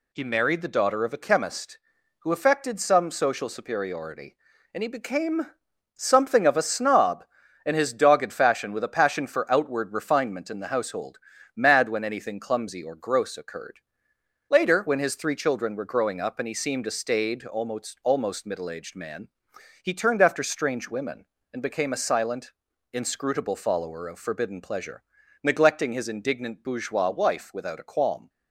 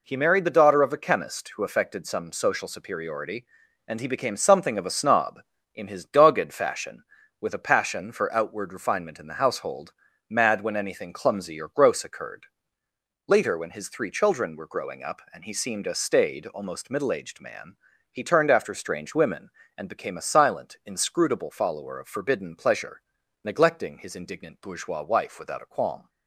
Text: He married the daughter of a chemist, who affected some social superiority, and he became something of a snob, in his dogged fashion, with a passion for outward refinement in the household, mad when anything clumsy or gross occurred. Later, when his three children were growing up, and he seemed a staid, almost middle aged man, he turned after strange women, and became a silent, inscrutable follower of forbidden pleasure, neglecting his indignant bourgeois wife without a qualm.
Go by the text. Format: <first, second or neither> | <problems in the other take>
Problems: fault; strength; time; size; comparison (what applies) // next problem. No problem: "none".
second | pauses between "became" and "something"; noticeable; at 5.4 s; 0.48 s long // says "almost" twice; at 18.0 s